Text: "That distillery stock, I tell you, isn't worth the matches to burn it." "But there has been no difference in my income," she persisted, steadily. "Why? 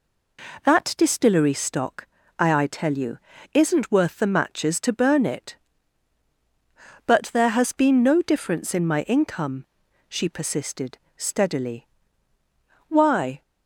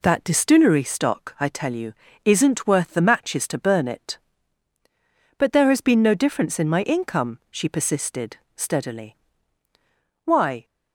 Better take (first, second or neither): second